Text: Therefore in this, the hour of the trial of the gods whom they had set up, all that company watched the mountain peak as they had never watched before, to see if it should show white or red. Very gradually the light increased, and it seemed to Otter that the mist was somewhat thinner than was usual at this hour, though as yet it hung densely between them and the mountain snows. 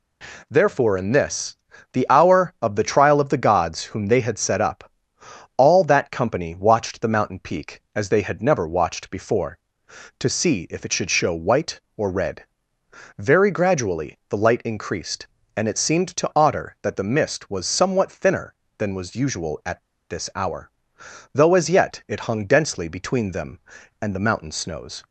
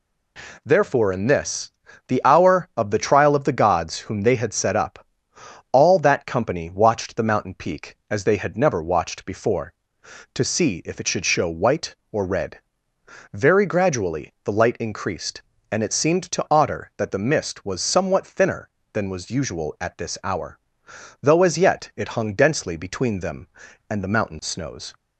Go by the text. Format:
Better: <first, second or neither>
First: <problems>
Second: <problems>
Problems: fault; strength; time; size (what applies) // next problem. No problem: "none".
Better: second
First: pauses between "at" and "this"; slight; at 19.8 s; 0.28 s long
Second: none